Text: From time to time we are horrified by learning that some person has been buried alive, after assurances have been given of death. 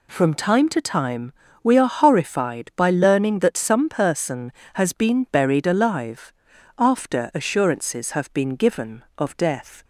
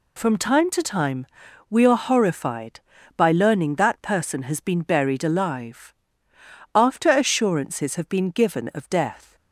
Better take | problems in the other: first | pauses between "time" and "we"; at 1.2 s; 0.42 s long; slight in the first // skips "some"; at 4.0 s

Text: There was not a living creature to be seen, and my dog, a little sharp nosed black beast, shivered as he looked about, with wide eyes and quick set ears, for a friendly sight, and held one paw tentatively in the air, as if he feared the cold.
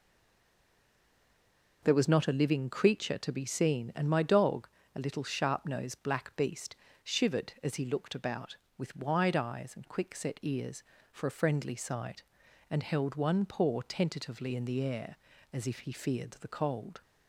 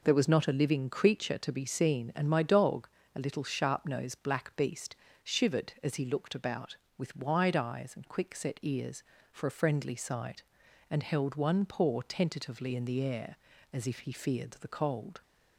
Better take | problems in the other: second | stays silent before the first word; noticeable; until 1.8 s; 1.8 s long

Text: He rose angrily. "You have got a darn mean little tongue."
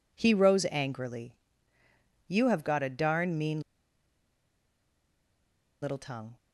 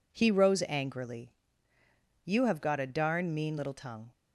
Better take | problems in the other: second | pauses between "mean" and "little"; strong; at 3.6 s; 2.2 s long

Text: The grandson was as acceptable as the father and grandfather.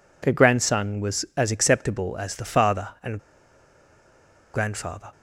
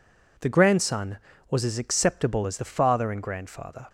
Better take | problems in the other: second | pauses between "and" and "grandfather"; strong; at 3.1 s; 1.3 s long

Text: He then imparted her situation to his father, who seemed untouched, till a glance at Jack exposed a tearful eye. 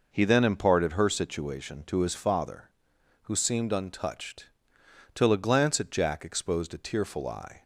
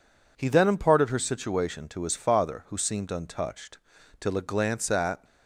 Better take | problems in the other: first | stops before "Jack exposed a tearful eye"; at 5.2 s

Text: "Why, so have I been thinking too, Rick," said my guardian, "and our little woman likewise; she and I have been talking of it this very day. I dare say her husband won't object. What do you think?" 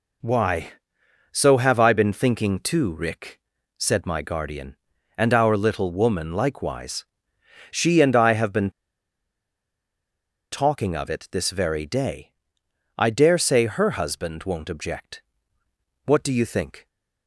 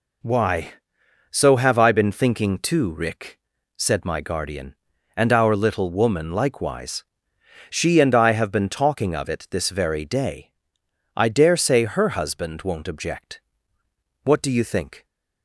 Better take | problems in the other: second | pauses between "been" and "talking"; strong; at 8.6 s; 1.8 s long

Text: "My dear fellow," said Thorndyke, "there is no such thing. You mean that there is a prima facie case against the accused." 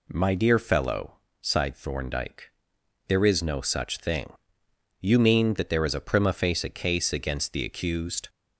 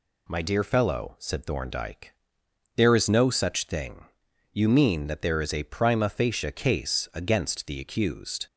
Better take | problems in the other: second | says "sighed" for "said"; at 1.4 s

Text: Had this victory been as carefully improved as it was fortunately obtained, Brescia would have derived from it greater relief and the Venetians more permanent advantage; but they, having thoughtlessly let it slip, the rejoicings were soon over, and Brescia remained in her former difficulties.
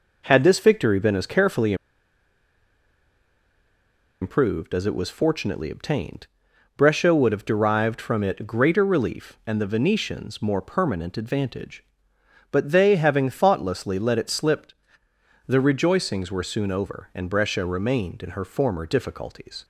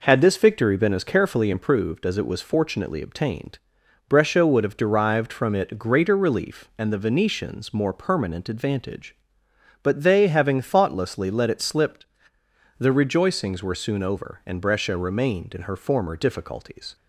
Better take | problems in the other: second | pauses between "carefully" and "improved"; strong; at 1.7 s; 2.4 s long

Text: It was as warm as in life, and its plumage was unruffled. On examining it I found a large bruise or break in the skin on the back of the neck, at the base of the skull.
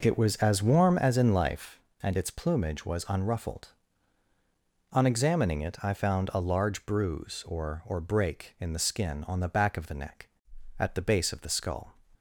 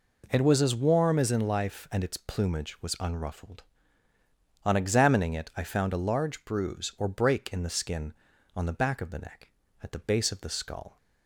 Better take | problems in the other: second | says "or" twice; at 7.8 s

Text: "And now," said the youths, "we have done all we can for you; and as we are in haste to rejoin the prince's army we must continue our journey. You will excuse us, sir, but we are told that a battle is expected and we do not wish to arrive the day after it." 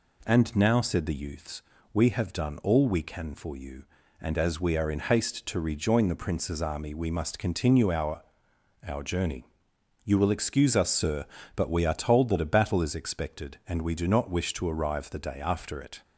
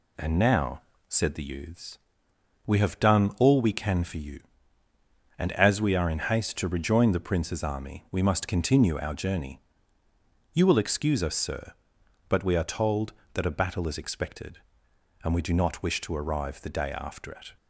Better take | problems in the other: second | says "our" twice; at 8.8 s

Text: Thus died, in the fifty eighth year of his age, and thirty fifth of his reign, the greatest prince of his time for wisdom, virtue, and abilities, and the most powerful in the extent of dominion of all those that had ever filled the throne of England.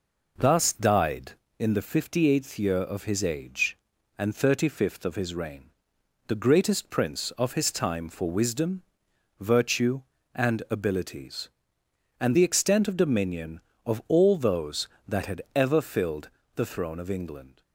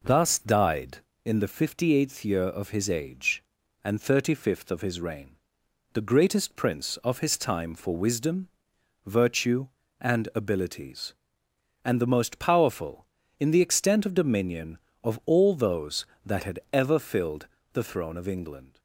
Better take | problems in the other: second | skips "the most powerful in"; at 12.3 s // pauses between "filled" and "the"; slight; at 16.2 s; 0.26 s long; slight in the second

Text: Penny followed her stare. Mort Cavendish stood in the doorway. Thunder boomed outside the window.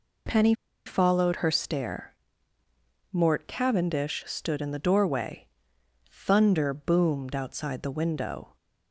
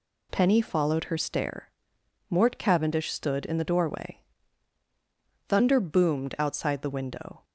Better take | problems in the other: second | pauses between "Penny" and "followed"; slight; at 0.5 s; 0.32 s long

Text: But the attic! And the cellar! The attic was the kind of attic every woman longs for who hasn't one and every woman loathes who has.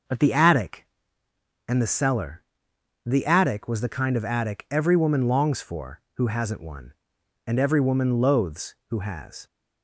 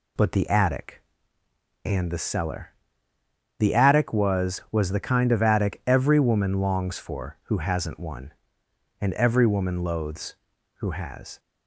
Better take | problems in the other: first | says "was" twice; at 4.7 s

